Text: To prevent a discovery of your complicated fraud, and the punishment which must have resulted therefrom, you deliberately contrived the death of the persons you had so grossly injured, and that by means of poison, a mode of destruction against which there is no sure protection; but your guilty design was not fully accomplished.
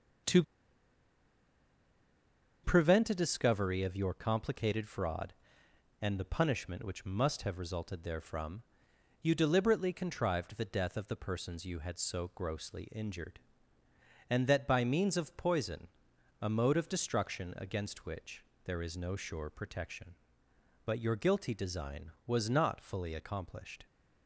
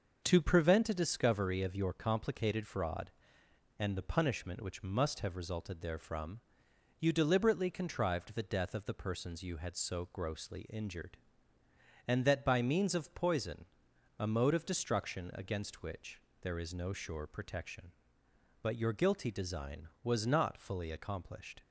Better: second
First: starts louder than the rest; until 3.4 s; 6.5 dB // pauses between "To" and "prevent"; strong; at 0.4 s; 2.2 s long // pauses between "which" and "there"; slight; at 18.4 s; 0.22 s long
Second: starts louder than the rest; noticeable; until 1.2 s; 6 dB // pauses between "which" and "there"; slight; at 16.1 s; 0.22 s long

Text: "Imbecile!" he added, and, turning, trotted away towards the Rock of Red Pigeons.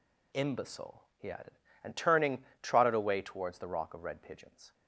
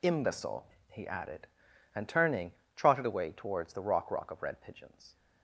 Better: first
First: none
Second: says "Rock" twice; at 4.1 s

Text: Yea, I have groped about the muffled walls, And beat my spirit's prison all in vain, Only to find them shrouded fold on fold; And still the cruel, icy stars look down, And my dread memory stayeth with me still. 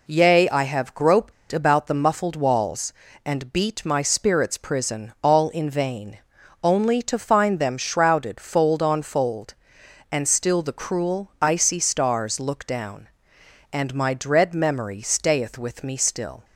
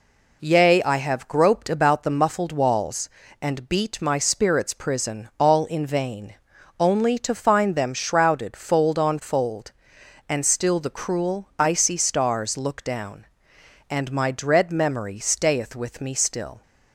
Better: second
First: pauses between "groped" and "about"; slight; at 1.3 s; 0.19 s long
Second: none

